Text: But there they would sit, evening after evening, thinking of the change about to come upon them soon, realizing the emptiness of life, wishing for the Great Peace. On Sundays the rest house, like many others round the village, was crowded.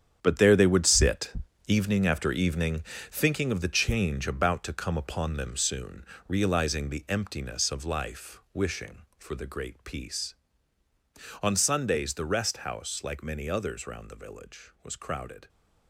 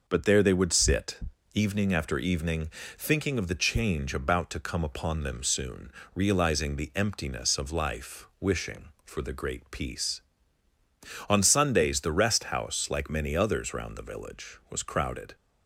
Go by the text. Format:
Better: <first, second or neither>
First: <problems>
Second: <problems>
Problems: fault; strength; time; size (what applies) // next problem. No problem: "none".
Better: second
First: gets quieter; strong; throughout; 11 dB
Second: none